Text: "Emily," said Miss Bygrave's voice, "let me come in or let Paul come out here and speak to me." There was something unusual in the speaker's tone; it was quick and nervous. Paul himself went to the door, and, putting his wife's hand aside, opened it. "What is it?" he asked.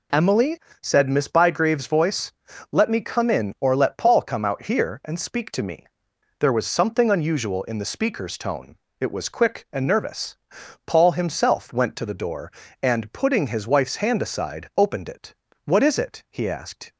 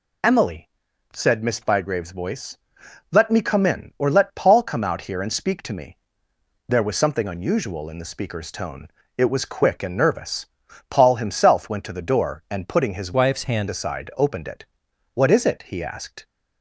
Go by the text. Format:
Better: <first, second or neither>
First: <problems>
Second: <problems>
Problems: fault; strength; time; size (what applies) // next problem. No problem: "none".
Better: first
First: none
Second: changes voice from "wife's" to "hand"; from 13.1 to 13.6 s; 0.5 s long